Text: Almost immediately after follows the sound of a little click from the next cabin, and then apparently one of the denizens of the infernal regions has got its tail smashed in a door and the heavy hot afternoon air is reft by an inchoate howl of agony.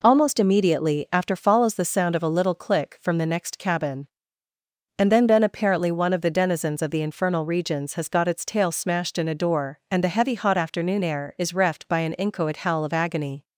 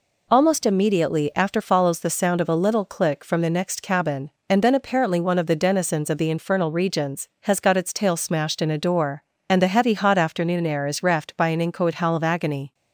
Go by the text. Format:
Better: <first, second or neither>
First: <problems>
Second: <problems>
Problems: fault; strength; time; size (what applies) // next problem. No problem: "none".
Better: second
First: says "then" twice; at 5.2 s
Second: none